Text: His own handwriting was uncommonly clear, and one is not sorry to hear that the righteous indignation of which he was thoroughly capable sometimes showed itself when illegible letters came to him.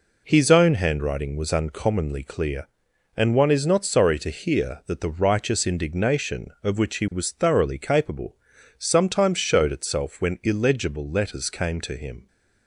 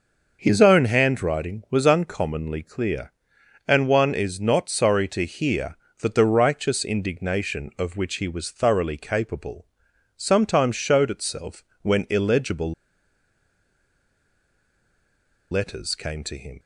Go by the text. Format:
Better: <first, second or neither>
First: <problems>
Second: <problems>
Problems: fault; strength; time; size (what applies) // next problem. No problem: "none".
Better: first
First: pauses between "capable" and "sometimes"; at 8.3 s; 0.42 s long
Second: pauses between "capable" and "sometimes"; noticeable; at 9.6 s; 0.50 s long // pauses between "itself" and "when"; slight; at 11.6 s; 0.20 s long // pauses between "illegible" and "letters"; strong; at 12.7 s; 2.7 s long